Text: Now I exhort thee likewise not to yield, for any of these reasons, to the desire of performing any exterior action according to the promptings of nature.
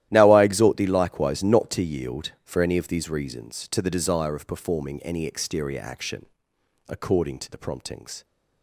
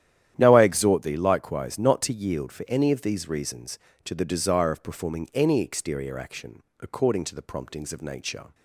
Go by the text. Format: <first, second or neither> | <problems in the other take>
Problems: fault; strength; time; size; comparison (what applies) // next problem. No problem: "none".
second | starts louder than the rest; strong; until 1.1 s; 13.5 dB; strong in the second // pauses between "action" and "according"; noticeable; at 6.2 s; 0.60 s long; slight in the second // stops before "of nature"; at 8.2 s